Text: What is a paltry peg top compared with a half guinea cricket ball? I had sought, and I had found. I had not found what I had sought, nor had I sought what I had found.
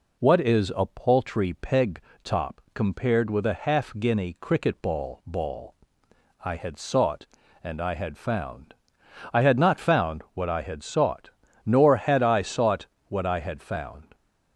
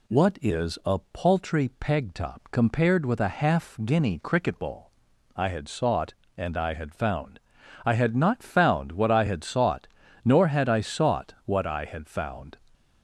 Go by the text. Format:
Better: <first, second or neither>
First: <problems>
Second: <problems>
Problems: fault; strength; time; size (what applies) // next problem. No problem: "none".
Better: second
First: pauses between "peg" and "top"; slight; at 1.9 s; 0.24 s long // says "ball" twice; at 5.2 s // pauses between "sought" and "what"; slight; at 12.8 s; 0.22 s long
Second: none